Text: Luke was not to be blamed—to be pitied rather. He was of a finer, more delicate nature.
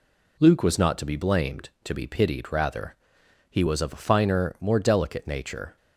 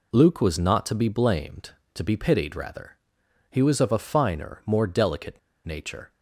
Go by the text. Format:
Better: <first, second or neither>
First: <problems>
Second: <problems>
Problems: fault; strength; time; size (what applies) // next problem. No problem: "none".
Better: first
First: none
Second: pauses between "delicate" and "nature"; slight; at 5.3 s; 0.26 s long